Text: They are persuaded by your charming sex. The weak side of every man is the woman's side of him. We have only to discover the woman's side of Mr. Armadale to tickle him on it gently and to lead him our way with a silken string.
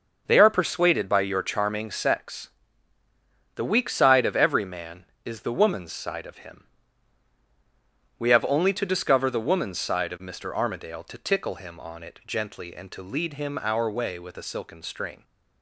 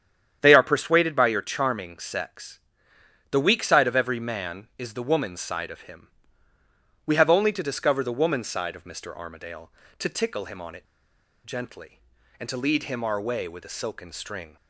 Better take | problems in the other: first | starts louder than the rest; strong; until 1.4 s; 9 dB // pauses between "it" and "gently"; noticeable; at 10.8 s; 0.60 s long

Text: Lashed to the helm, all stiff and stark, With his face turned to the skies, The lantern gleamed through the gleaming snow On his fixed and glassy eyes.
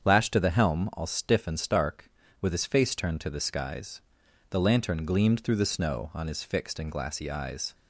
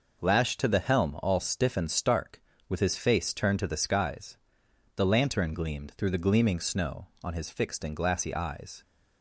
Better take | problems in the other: second | starts louder than the rest; strong; until 1.0 s; 7.5 dB // skips "gleaming"; at 5.6 s

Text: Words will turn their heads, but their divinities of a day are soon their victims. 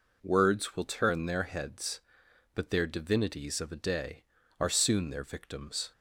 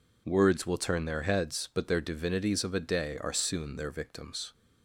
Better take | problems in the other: neither | none

